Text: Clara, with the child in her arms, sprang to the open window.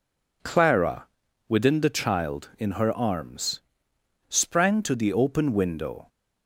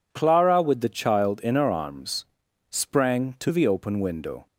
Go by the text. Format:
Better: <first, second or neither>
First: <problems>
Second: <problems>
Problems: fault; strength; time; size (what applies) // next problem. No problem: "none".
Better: second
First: says "within" for "with"; at 1.4 s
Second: none